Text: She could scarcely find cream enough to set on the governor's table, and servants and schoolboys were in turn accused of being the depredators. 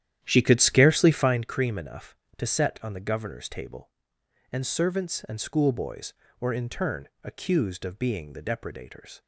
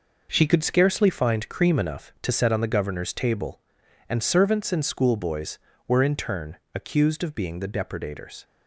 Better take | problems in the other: second | starts louder than the rest; strong; until 1.4 s; 11 dB // pauses between "turn" and "accused"; slight; at 7.0 s; 0.16 s long; slight in the second

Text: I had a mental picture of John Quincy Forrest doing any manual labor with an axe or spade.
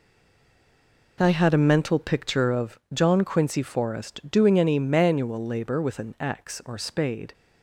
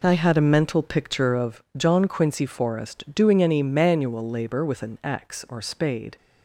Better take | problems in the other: second | stays silent before the first word; until 1.1 s; 1.1 s long

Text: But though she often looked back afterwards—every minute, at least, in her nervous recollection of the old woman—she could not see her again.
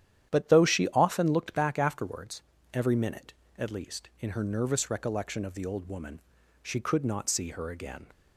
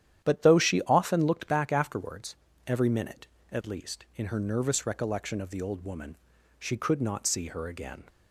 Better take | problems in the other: neither | starts louder than the rest; strong; the same in both

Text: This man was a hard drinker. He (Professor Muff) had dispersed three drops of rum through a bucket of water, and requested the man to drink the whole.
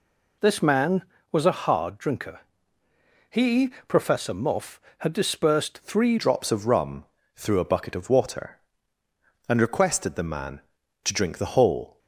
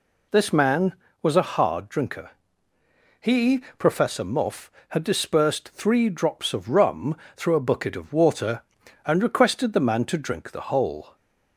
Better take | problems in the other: second | changes voice at "drops"; from 6.1 s on; 5.8 s long // pauses between "rum" and "through"; slight; at 7.0 s; 0.30 s long; slight in the second

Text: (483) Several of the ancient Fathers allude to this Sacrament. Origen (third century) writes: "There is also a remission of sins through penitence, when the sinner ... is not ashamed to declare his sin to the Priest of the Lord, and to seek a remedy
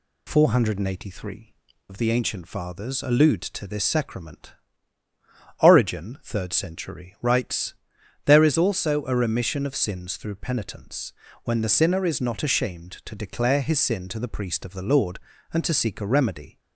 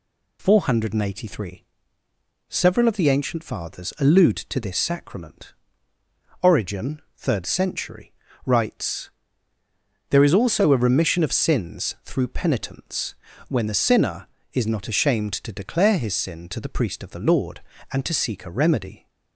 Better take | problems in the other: second | skips "Several"; at 1.7 s

